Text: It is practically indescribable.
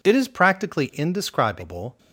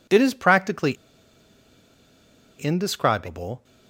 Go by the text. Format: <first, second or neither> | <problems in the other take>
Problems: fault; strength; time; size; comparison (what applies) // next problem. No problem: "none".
first | pauses between "practically" and "indescribable"; strong; at 0.9 s; 1.6 s long